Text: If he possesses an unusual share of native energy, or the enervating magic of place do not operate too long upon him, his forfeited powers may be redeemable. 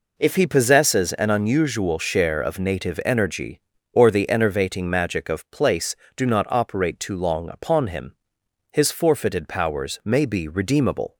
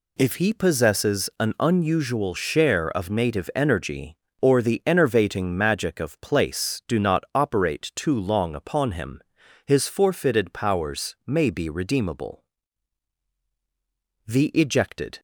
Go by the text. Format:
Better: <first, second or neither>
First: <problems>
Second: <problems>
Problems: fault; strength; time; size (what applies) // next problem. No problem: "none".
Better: first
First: none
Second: goes on to say "The ejected"; noticeable; from 14.2 s on; 0.94 s long